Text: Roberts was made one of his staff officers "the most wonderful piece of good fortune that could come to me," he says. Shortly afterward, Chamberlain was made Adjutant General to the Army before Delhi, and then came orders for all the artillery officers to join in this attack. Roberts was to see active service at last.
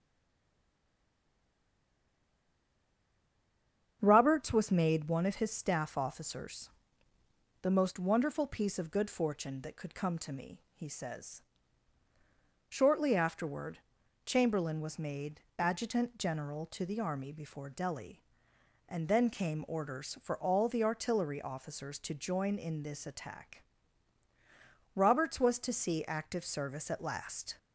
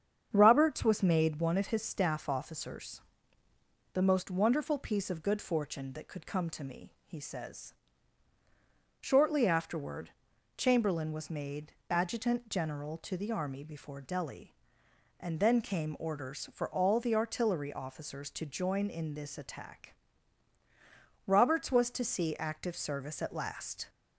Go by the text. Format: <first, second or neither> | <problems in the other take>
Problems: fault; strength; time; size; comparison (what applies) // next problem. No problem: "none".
second | stays silent before the first word; strong; until 4.0 s; 4.0 s long // starts louder than the rest; strong; until 5.0 s; 8 dB; strong in the second // pauses between "officers" and "the"; noticeable; at 6.6 s; 0.94 s long; noticeable in the second // pauses between "made" and "Adjutant"; slight; at 15.4 s; 0.16 s long; slight in the second